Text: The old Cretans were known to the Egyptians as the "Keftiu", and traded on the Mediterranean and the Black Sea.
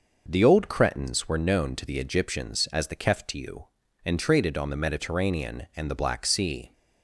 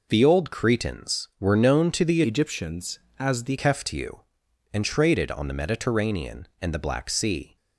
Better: first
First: none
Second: changes voice from "Egyptians" to "the"; from 2.2 to 3.5 s; 1.3 s long

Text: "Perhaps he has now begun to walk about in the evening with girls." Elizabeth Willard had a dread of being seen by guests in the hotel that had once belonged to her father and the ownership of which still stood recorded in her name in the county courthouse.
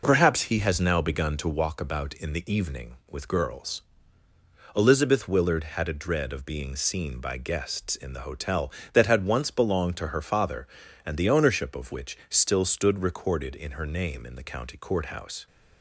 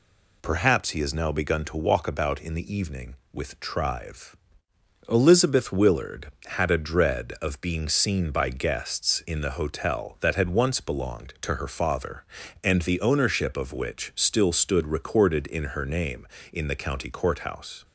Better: first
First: none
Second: says "trive" for "girls"; at 3.5 s

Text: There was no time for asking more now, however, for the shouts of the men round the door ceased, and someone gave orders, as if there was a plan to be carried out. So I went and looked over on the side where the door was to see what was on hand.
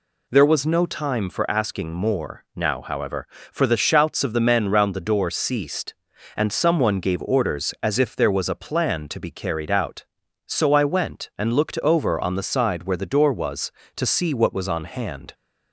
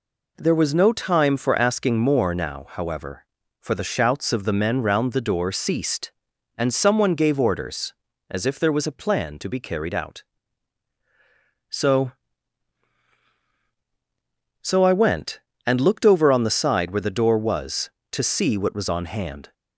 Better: first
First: none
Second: says "So" twice; at 14.6 s

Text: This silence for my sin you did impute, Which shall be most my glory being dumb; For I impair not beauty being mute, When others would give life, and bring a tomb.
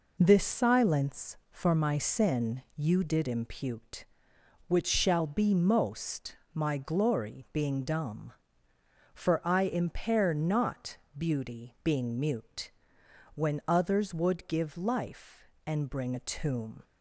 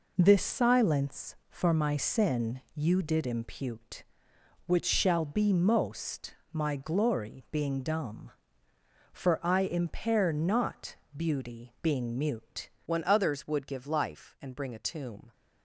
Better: first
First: pauses between "most" and "my"; slight; at 6.3 s; 0.20 s long // pauses between "not" and "beauty"; slight; at 10.9 s; 0.18 s long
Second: pauses between "most" and "my"; slight; at 6.3 s; 0.20 s long // pauses between "not" and "beauty"; slight; at 10.9 s; 0.18 s long // changes voice at "When"; from 12.8 s on; 2.5 s long

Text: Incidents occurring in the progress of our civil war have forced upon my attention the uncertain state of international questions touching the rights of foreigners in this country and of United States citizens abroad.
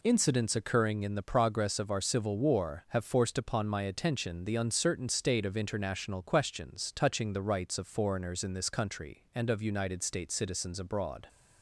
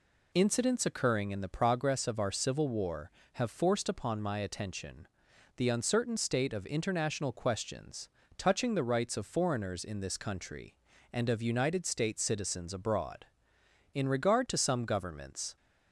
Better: first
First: none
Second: pauses between "attention" and "the"; noticeable; at 5.0 s; 0.48 s long // pauses between "questions" and "touching"; slight; at 8.0 s; 0.30 s long // goes on to say "In regard to some governments"; from 13.9 s on; 1.6 s long

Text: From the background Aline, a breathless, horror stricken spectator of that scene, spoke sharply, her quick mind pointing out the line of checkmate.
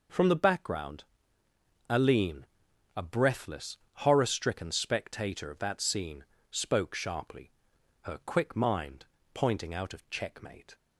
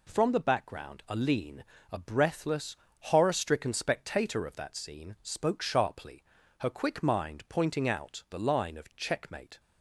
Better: second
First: pauses between "background" and "Aline"; noticeable; at 1.0 s; 0.84 s long // pauses between "mind" and "pointing"; slight; at 9.0 s; 0.28 s long // skips "the line"; at 9.9 s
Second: none

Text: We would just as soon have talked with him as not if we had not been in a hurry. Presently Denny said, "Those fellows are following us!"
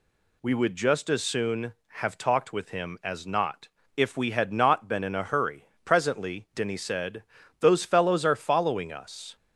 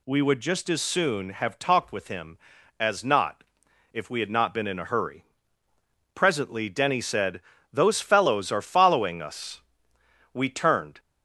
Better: first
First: pauses between "not" and "if"; slight; at 3.6 s; 0.30 s long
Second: pauses between "not" and "if"; noticeable; at 3.4 s; 0.50 s long // goes on to say "We turned"; noticeable; from 10.3 s on; 0.66 s long

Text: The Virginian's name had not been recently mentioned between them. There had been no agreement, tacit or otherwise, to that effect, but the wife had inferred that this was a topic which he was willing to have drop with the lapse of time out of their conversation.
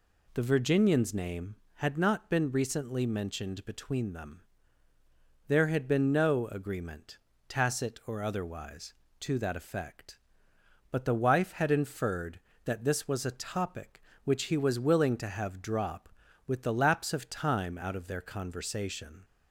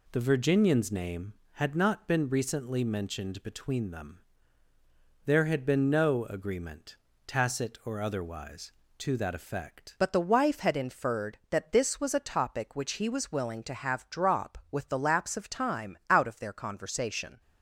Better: first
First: none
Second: changes voice at "but"; from 9.9 s on; 7.5 s long

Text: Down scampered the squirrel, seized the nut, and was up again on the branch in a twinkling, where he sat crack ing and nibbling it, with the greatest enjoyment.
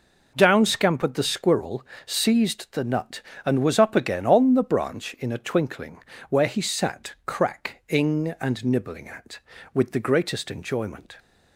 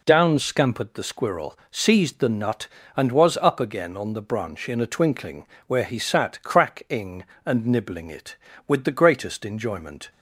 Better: second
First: says "at" for "it"; at 9.0 s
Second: none

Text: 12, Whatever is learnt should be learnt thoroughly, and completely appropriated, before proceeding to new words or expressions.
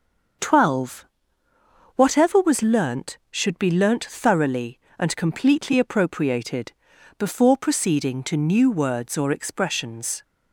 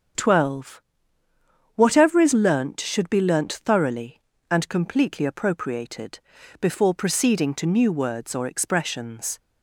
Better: second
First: starts louder than the rest; until 2.3 s; 6.5 dB // says "was" for "is"; at 2.3 s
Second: starts louder than the rest; strong; until 2.1 s; 7.5 dB

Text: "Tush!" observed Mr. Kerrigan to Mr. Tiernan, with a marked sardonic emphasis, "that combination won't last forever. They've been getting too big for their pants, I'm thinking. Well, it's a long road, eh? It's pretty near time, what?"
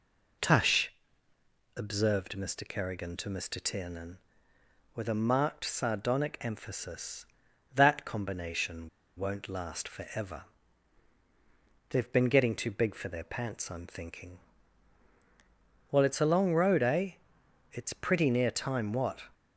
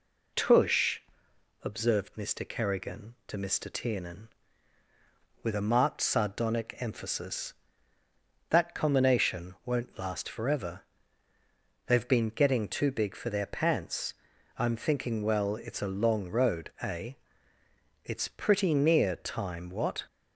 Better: second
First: pauses between "combination" and "won't"; slight; at 8.8 s; 0.27 s long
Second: none

